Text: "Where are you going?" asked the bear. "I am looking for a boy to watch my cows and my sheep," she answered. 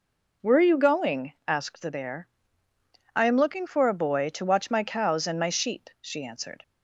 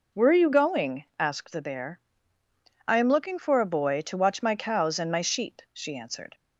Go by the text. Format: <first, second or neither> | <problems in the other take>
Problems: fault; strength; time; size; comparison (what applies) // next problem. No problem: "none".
neither | none